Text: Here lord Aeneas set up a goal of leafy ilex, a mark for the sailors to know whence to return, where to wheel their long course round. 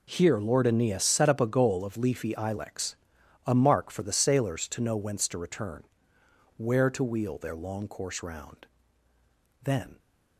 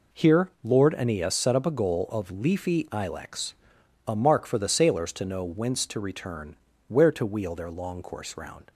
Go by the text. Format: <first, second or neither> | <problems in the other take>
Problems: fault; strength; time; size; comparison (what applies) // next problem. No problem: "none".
second | goes on to say "Then"; slight; from 9.6 s on; 0.36 s long